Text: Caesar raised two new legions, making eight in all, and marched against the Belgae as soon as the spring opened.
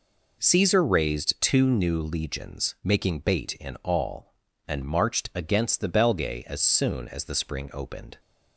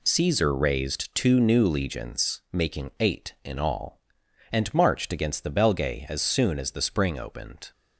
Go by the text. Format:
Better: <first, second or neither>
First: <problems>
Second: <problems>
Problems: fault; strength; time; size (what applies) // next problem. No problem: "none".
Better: second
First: says "bait" for "eight"; at 3.1 s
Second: none